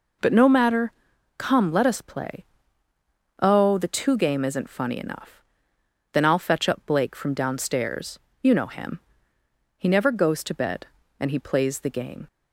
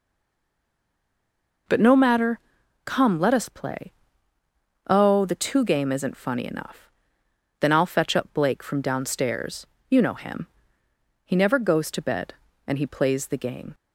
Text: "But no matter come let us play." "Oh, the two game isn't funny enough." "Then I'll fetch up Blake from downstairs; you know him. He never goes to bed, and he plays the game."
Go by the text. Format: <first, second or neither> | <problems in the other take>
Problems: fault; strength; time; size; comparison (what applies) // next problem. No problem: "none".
first | stays silent before the first word; noticeable; until 1.6 s; 1.6 s long // pauses between "matter" and "come"; noticeable; at 2.3 s; 0.46 s long; noticeable in the first